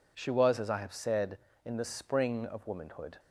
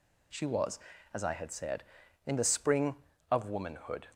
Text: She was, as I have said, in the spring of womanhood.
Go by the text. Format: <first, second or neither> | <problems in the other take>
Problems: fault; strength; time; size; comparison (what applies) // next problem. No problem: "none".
first | says "had" for "have"; at 1.3 s